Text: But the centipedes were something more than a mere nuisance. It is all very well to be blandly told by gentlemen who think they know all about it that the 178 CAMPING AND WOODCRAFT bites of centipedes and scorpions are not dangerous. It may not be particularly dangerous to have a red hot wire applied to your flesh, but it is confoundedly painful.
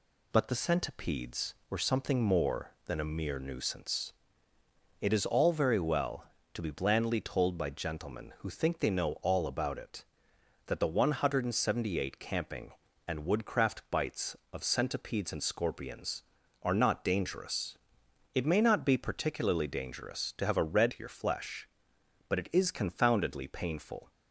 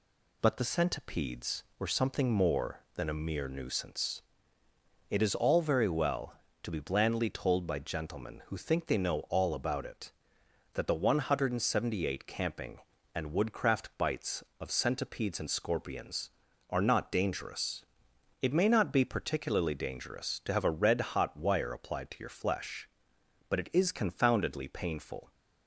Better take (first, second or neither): second